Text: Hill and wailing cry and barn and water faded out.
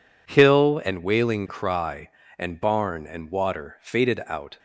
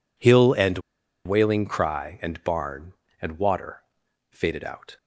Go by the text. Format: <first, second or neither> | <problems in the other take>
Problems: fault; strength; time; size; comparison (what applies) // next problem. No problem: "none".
first | pauses between "and" and "wailing"; noticeable; at 0.7 s; 0.46 s long // pauses between "water" and "faded"; noticeable; at 3.8 s; 0.48 s long